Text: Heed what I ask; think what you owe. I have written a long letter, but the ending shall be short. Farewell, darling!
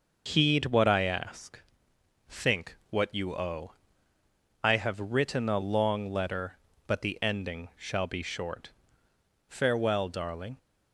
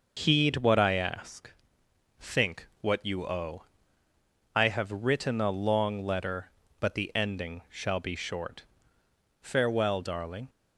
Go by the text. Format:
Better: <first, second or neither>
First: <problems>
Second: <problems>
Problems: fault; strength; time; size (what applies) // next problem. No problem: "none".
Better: neither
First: pauses between "think" and "what"; slight; at 2.7 s; 0.16 s long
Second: pauses between "think" and "what"; slight; at 2.6 s; 0.16 s long